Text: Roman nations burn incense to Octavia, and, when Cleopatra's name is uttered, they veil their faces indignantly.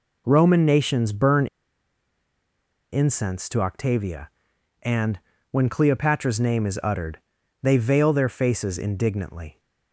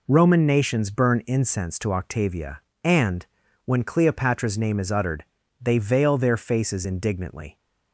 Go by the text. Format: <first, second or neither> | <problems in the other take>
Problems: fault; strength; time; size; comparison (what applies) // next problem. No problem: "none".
second | pauses between "burn" and "incense"; strong; at 1.4 s; 1.4 s long